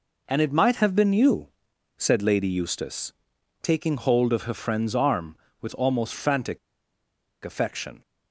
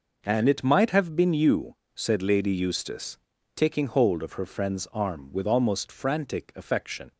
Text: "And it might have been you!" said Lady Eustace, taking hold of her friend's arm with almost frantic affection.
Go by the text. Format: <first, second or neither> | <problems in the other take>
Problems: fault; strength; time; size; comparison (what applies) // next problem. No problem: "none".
second | pauses between "frantic" and "affection"; noticeable; at 6.5 s; 0.86 s long